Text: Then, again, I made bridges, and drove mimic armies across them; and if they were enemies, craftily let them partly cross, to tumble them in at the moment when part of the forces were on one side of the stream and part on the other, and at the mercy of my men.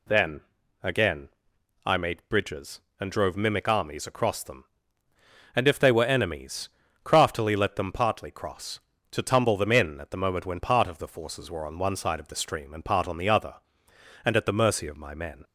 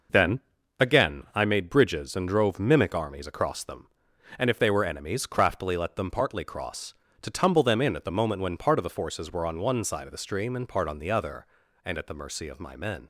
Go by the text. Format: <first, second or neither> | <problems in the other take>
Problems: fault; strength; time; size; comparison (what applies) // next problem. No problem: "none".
neither | none